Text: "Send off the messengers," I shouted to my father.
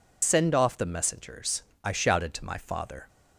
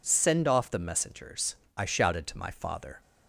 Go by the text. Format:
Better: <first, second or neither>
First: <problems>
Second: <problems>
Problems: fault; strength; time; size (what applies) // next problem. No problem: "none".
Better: second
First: loses the start of "Send"; at 0.2 s; 120 ms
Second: none